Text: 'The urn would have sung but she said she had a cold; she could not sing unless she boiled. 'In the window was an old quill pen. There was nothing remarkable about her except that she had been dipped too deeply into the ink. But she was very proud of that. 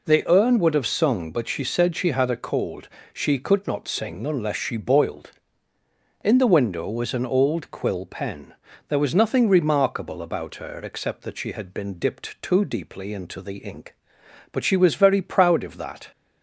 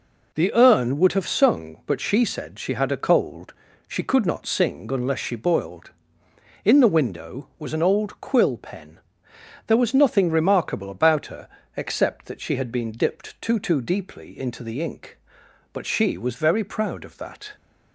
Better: first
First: none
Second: pauses between "her" and "except"; slight; at 11.5 s; 0.26 s long // says "too" twice; at 13.5 s

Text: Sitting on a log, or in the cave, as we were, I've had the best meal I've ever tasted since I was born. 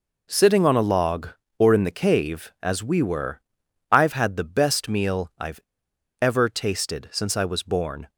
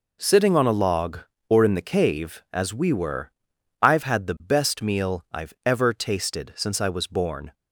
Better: second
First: pauses between "I've" and "ever"; noticeable; at 5.5 s; 0.63 s long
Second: none

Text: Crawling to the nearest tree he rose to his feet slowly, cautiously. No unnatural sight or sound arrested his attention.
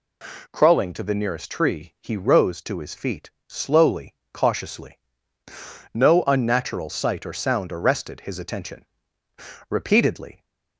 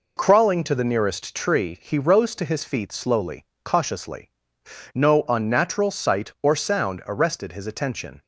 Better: second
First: pauses between "feet" and "slowly"; slight; at 3.3 s; 0.18 s long // goes on to say "Repeatedly"; noticeable; from 9.6 s on; 0.76 s long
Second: none

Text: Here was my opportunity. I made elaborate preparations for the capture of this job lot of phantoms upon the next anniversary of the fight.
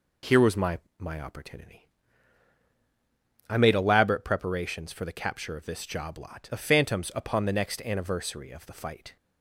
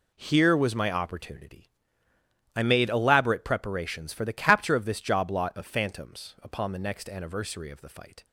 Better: second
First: says "my" twice; at 0.9 s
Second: none

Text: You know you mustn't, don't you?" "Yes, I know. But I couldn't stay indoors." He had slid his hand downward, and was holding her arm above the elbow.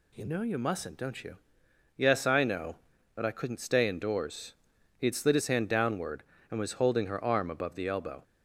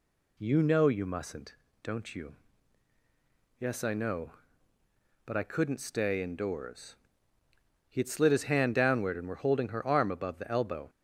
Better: first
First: none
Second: says "were" for "was"; at 9.2 s

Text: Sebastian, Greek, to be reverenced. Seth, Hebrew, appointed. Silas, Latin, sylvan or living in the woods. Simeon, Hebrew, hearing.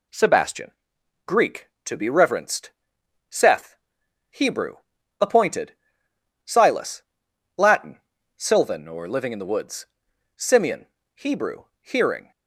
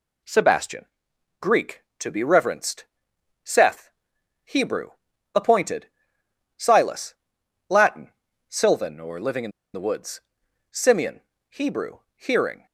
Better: first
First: none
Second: pauses between "in" and "the"; slight; at 9.5 s; 0.23 s long

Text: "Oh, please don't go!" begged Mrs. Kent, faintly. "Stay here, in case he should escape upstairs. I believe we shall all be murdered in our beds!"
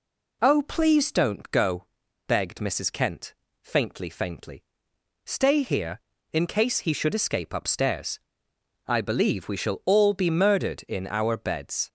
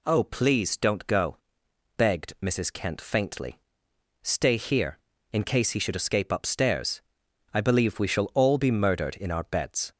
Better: second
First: says "faintly" twice; at 4.0 s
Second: none

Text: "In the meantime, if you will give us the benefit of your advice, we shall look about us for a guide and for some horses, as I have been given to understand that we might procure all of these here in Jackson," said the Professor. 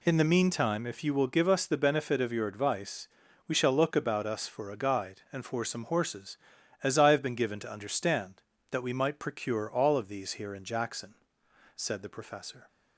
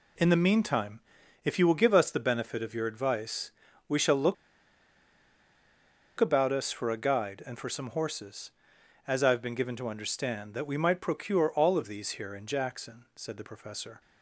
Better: first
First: none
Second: pauses between "look" and "about"; strong; at 4.3 s; 1.8 s long

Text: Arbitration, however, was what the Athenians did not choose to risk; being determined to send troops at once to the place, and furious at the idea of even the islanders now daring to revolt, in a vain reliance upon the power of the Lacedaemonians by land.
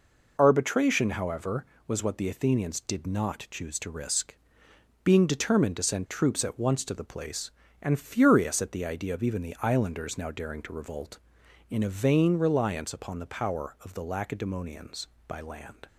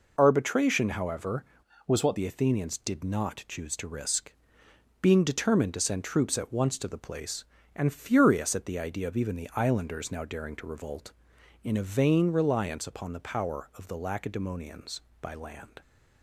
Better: first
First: none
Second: changes voice from "was" to "what"; from 1.8 to 2.1 s; 0.3 s long

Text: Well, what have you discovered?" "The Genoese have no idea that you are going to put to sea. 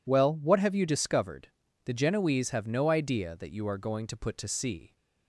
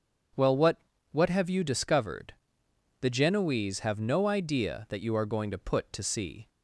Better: first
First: none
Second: starts louder than the rest; strong; until 1.7 s; 7.5 dB // says "what" twice; at 1.1 s

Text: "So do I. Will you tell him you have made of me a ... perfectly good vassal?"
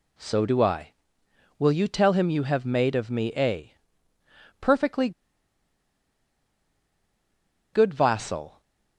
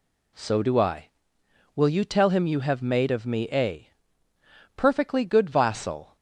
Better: second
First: pauses between "perfectly" and "good"; strong; at 5.1 s; 2.6 s long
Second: none

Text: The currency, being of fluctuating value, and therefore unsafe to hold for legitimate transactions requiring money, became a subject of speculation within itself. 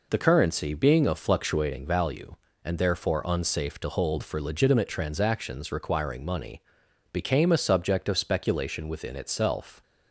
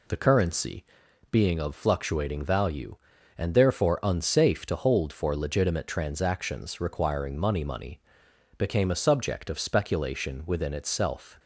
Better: first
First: none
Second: says "money" twice; at 7.6 s

